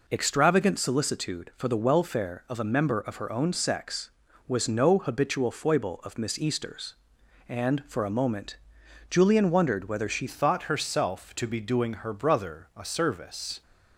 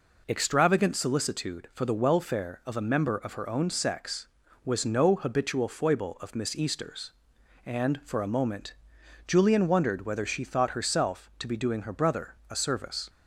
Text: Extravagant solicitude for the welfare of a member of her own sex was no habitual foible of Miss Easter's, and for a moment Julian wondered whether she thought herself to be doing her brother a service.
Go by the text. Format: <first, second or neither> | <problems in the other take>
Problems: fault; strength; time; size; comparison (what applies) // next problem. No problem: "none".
second | pauses between "moment" and "Julian"; noticeable; at 8.5 s; 0.54 s long; noticeable in the second // changes voice at "thought"; from 10.2 s on; 3.4 s long